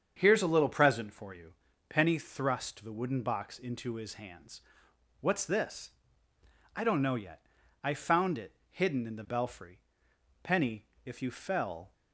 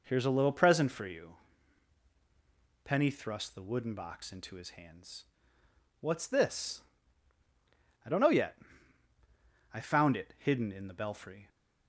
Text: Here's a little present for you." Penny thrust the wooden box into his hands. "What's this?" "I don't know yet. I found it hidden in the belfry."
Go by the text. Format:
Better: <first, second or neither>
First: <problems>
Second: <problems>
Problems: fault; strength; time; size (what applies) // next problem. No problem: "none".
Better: second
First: starts louder than the rest; strong; until 1.1 s; 7.5 dB // pauses between "it" and "hidden"; slight; at 8.5 s; 0.16 s long // goes on to say "Penny if you fell"; from 10.4 s on; 1.5 s long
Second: none